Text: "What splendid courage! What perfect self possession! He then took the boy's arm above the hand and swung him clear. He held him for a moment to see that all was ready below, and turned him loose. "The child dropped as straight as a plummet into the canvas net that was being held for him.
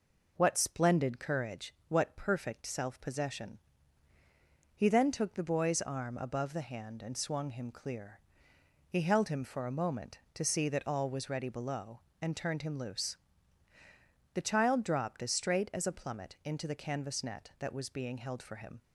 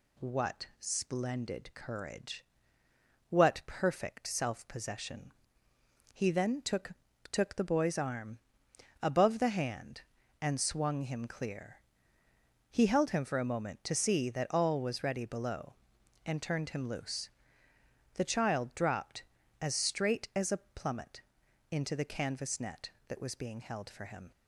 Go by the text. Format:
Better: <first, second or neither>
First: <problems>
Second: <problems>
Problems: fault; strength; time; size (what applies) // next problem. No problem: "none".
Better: first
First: none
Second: says "took" twice; at 7.3 s // pauses between "arm" and "above"; noticeable; at 8.3 s; 0.64 s long // pauses between "plummet" and "into"; noticeable; at 21.2 s; 0.48 s long